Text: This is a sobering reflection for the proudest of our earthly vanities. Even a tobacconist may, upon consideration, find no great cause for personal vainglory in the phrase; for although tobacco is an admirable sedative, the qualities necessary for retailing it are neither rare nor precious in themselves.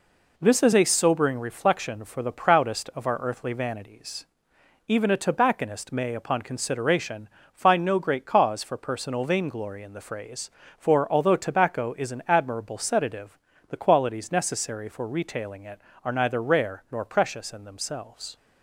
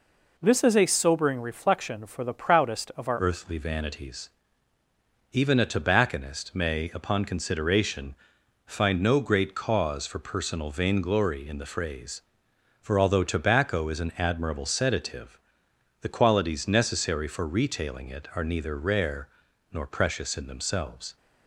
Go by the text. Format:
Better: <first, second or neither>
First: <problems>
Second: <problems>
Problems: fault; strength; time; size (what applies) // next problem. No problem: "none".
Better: first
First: none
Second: changes voice at "earthly"; from 3.1 s on; 18.0 s long // pauses between "rare" and "nor"; noticeable; at 19.2 s; 0.46 s long